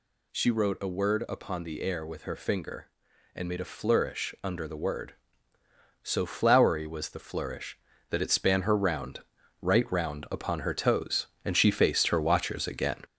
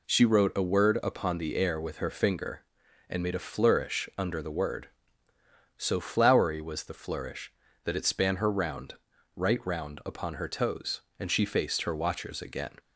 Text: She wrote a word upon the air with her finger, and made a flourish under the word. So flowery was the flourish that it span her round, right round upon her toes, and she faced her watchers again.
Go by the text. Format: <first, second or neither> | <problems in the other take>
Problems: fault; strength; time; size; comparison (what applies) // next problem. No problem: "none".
second | gets louder; noticeable; throughout; 5 dB